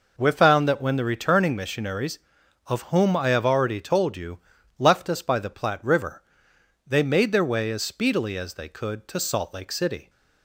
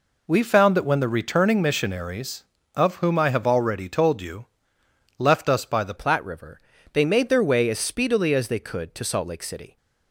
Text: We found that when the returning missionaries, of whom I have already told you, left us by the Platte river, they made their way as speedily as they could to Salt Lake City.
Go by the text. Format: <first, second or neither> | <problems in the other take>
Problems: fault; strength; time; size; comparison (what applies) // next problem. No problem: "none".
first | changes voice at "Platte"; from 5.9 s on; 3.8 s long